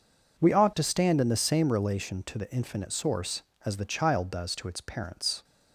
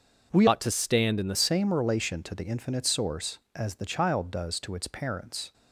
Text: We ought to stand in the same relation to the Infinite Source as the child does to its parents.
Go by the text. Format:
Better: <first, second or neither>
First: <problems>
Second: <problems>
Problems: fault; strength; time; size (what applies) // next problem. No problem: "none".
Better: first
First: none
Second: starts louder than the rest; until 1.3 s; 6.5 dB // changes voice from "ought" to "the"; from 0.4 to 1.3 s; 0.9 s long